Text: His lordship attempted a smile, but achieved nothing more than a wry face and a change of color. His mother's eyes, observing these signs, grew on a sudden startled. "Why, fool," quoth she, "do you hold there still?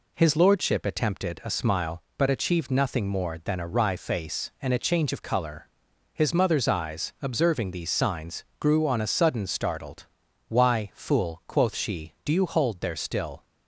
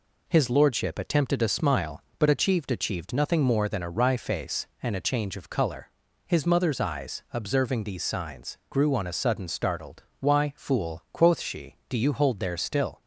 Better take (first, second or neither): first